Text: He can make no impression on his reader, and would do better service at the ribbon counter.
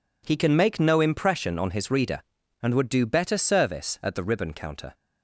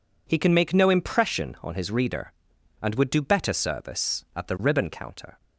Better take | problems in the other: neither | none

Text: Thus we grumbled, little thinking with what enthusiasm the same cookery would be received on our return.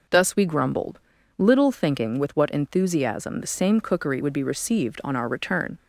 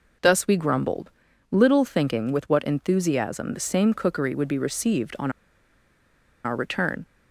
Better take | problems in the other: first | pauses between "on" and "our"; at 5.3 s; 1.1 s long

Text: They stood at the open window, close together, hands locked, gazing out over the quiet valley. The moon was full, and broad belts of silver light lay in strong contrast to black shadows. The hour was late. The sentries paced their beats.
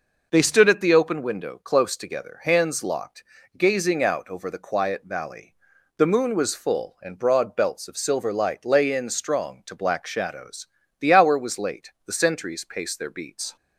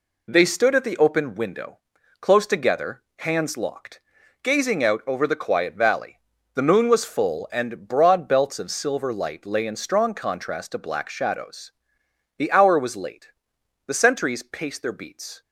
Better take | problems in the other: second | skips "contrast"; at 9.6 s

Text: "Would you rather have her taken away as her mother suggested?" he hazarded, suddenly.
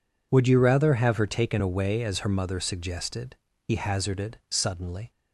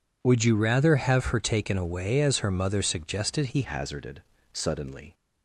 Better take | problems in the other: first | changes voice at "hazarded"; from 3.6 s on; 1.5 s long

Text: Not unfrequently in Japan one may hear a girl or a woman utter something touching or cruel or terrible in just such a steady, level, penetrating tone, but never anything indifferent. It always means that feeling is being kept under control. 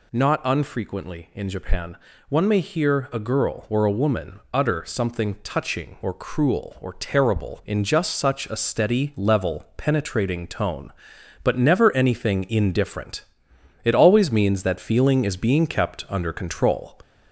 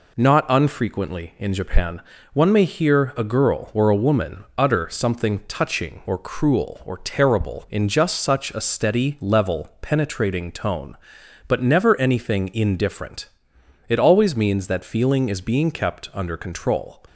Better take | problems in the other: second | gets louder; slight; throughout; 2.5 dB // pauses between "Japan" and "one"; slight; at 1.9 s; 0.34 s long; slight in the second

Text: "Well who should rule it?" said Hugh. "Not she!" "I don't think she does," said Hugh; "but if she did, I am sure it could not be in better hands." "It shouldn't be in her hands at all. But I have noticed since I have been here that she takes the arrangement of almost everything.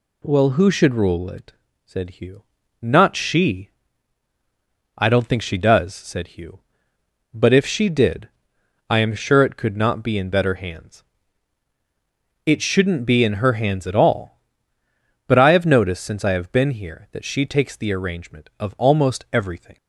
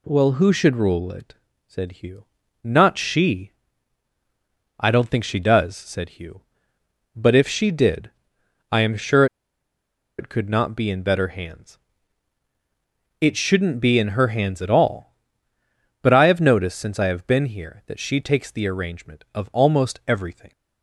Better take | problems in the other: first | pauses between "sure" and "it"; noticeable; at 9.2 s; 0.93 s long

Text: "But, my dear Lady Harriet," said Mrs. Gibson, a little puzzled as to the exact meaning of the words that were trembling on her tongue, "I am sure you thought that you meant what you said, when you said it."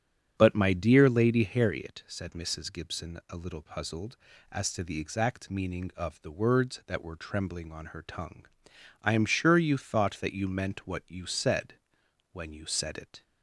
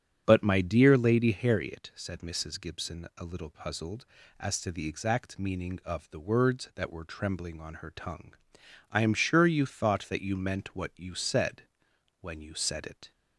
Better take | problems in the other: neither | starts louder than the rest; strong; the same in both

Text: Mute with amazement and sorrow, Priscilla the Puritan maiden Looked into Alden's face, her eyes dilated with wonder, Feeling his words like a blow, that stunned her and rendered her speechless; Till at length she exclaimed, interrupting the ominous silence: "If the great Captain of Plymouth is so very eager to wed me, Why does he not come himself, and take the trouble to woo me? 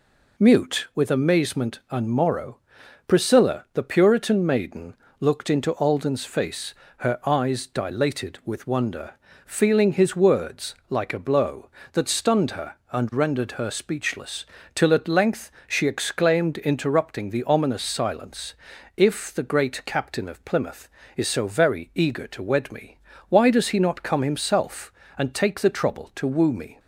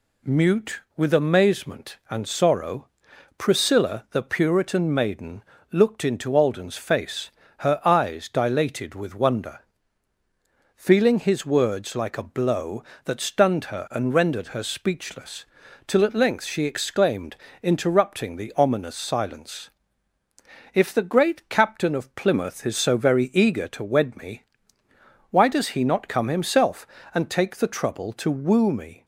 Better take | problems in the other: second | says "morrow" for "sorrow"; at 2.0 s // pauses between "maiden" and "Looked"; slight; at 4.9 s; 0.26 s long; slight in the second // pauses between "length" and "she"; slight; at 15.4 s; 0.18 s long

